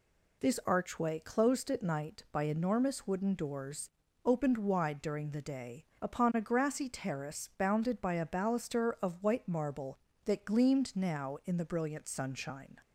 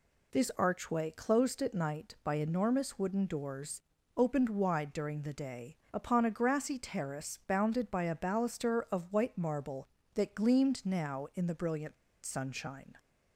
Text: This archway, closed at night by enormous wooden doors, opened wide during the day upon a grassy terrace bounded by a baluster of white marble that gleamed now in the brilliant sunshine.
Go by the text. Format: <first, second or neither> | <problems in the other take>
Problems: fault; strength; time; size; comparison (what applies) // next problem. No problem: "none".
first | pauses between "day" and "upon"; slight; at 5.7 s; 0.16 s long; slight in the first // pauses between "brilliant" and "sunshine"; slight; at 11.9 s; 0.29 s long